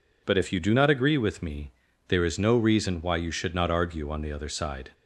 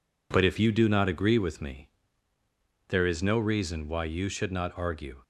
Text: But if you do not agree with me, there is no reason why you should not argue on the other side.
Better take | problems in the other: first | stops before "on the other side"; at 5.2 s

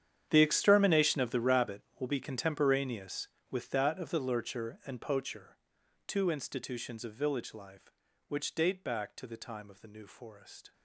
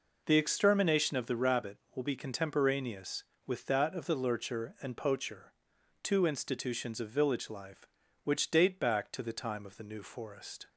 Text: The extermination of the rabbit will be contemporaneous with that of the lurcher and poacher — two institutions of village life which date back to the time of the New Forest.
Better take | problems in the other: second | gets quieter; strong; throughout; 19 dB

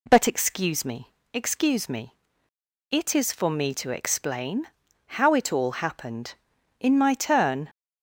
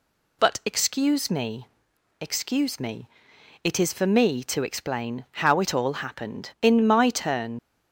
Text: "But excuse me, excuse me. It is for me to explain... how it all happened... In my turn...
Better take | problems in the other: first | leaves "turn" unfinished; at 7.5 s; 50 ms

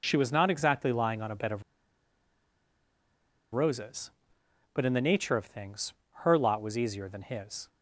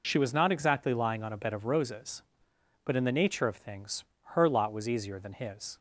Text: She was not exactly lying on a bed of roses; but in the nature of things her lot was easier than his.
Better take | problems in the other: second | pauses between "of" and "roses"; strong; at 1.6 s; 1.9 s long // pauses between "things" and "her"; slight; at 5.9 s; 0.30 s long; slight in the second

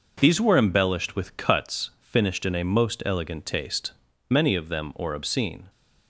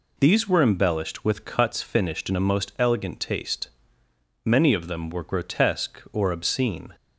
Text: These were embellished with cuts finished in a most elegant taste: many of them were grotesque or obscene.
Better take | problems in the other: second | skips "were grotesque"; at 4.9 s

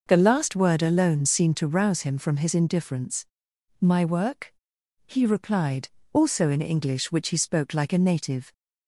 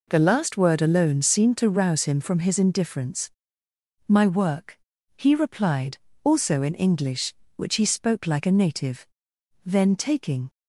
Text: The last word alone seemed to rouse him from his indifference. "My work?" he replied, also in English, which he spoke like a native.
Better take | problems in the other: first | goes on to say "Then taking"; noticeable; from 9.6 s on; 0.84 s long

